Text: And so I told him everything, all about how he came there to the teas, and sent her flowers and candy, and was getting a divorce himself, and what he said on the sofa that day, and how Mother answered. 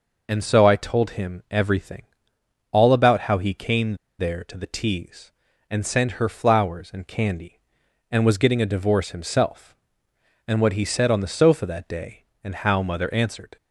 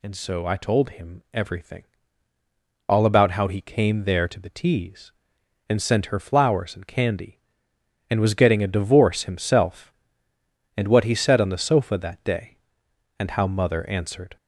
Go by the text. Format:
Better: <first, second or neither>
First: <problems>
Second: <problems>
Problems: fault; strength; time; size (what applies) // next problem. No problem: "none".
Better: second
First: pauses between "came" and "there"; slight; at 3.9 s; 0.24 s long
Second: none